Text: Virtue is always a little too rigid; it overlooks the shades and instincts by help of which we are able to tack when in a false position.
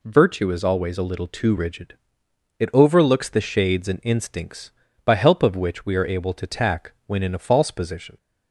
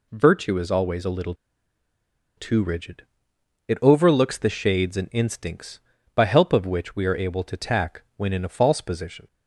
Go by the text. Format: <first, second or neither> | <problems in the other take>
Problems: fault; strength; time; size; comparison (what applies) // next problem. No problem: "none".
first | pauses between "little" and "too"; at 1.3 s; 1.0 s long